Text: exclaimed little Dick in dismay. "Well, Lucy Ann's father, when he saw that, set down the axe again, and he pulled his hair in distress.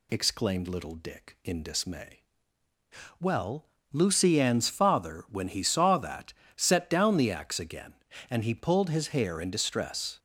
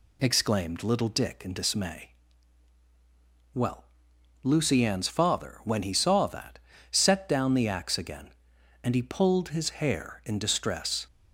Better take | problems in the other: neither | none

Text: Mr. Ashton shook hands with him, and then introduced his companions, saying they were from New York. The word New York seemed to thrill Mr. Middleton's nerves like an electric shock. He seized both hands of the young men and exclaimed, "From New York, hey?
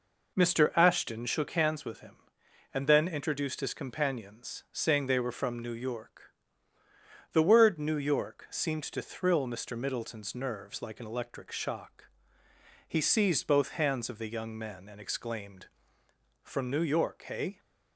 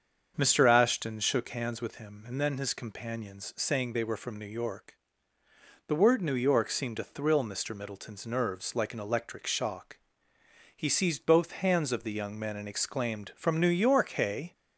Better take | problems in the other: first | starts louder than the rest; strong; until 1.3 s; 7 dB // skips "introduced"; at 2.5 s

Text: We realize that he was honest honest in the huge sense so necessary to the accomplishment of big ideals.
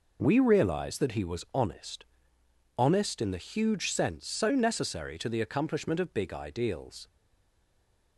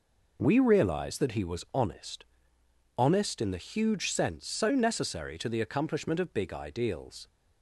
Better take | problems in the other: second | pauses between "honest" and "honest"; noticeable; at 2.0 s; 0.72 s long; noticeable in the second // stays silent after the last word; from 7.0 s on; 1.1 s long

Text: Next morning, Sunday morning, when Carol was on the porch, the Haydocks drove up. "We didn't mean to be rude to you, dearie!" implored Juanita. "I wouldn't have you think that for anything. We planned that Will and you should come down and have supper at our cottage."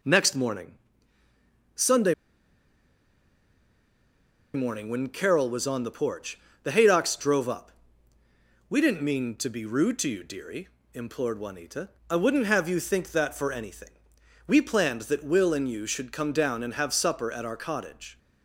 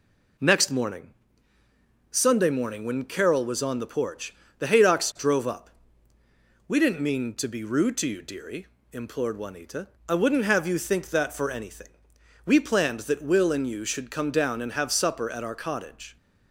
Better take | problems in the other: second | pauses between "Sunday" and "morning"; strong; at 2.1 s; 2.4 s long

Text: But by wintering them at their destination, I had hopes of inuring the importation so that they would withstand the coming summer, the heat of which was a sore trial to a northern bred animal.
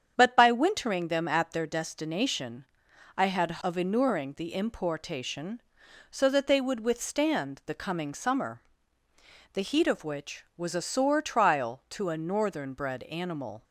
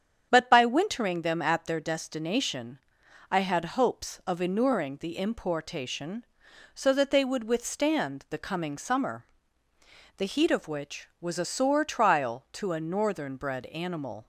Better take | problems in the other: second | starts louder than the rest; strong; until 1.1 s; 8 dB; strong in the second // skips "hopes"; at 3.6 s

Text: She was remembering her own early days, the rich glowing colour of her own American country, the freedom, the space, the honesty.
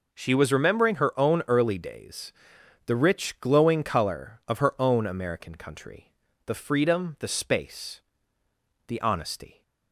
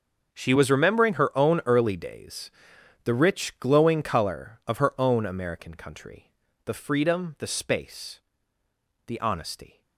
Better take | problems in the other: first | gets quieter; strong; throughout; 15.5 dB

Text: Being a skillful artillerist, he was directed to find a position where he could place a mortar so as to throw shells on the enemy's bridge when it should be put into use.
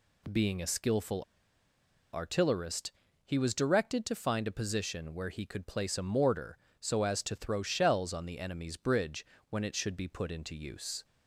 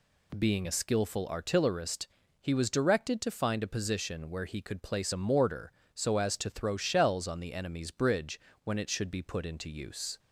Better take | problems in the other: second | pauses between "skillful" and "artillerist"; noticeable; at 1.2 s; 0.91 s long // pauses between "bridge" and "when"; slight; at 9.2 s; 0.24 s long; slight in the second

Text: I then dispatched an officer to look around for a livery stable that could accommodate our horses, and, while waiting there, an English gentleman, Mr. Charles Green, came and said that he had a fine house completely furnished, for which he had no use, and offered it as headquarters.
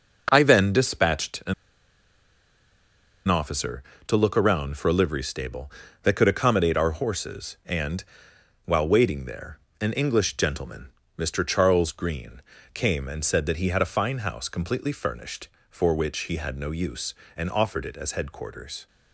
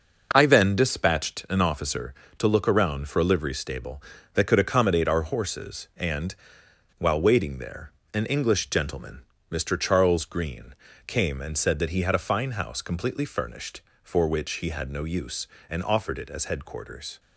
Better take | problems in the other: second | pauses between "an" and "officer"; strong; at 1.5 s; 1.7 s long

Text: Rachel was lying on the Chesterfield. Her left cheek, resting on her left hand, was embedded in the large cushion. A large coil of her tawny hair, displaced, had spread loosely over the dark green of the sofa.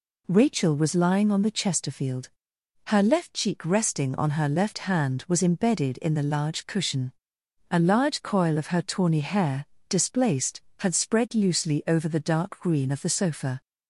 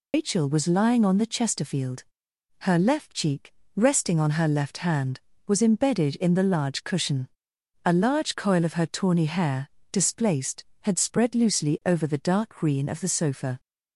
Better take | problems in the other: first | loses the start of "Rachel"; at 0.1 s; 130 ms

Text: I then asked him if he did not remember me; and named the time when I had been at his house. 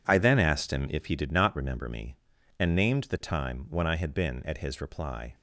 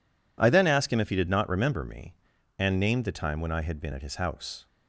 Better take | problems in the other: second | says "reply" for "house"; at 4.8 s

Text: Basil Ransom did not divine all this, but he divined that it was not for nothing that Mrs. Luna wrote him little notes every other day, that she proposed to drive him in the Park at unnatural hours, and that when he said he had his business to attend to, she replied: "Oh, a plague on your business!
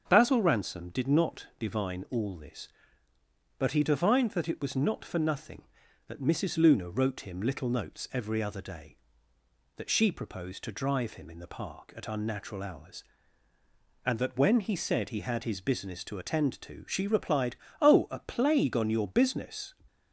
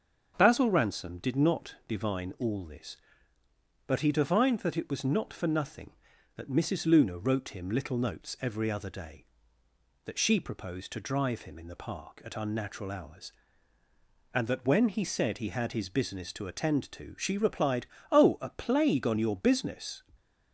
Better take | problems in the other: neither | starts louder than the rest; the same in both

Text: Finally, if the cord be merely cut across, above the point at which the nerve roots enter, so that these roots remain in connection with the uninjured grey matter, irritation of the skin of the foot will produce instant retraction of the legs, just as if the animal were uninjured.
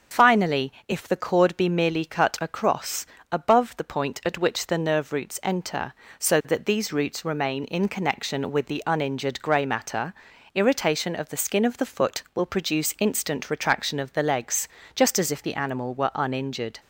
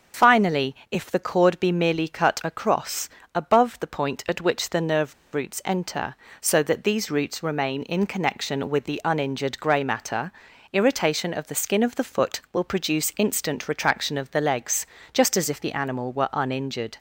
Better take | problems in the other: first | starts louder than the rest; until 1.4 s; 6.5 dB; also in the first // pauses between "nerve" and "roots"; slight; at 5.1 s; 0.19 s long

